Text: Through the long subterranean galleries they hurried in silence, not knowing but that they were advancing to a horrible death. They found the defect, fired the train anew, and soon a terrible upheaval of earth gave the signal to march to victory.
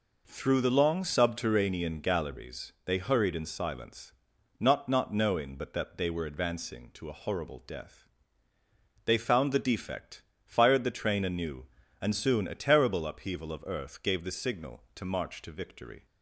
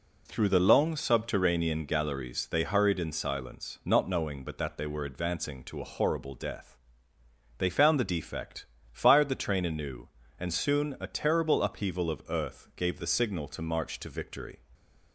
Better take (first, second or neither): second